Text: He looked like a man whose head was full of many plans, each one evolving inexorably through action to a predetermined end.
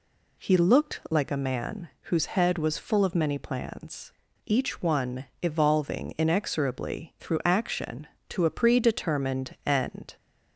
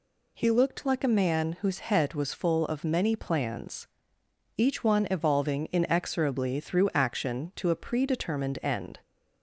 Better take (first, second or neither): neither